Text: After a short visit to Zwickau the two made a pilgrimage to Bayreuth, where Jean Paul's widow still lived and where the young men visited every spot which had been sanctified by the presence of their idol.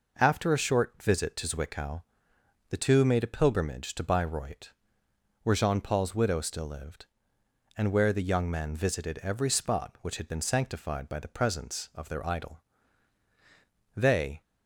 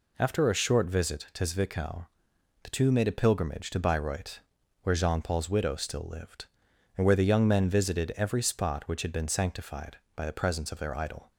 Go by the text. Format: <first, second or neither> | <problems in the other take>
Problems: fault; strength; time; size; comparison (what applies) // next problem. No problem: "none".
second | pauses between "Zwickau" and "the"; noticeable; at 2.0 s; 0.66 s long; noticeable in the second // goes on to say "They"; slight; from 13.9 s on; 0.46 s long